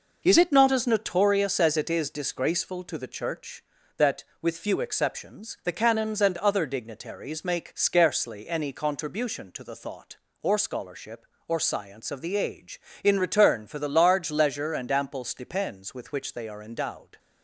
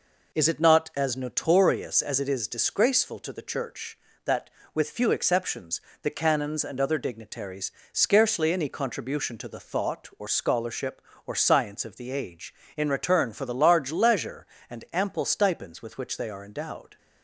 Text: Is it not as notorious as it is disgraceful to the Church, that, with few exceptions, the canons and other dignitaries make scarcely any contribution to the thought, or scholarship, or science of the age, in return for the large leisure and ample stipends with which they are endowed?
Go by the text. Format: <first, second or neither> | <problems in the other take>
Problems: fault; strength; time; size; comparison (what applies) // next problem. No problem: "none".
first | skips "make"; at 7.8 s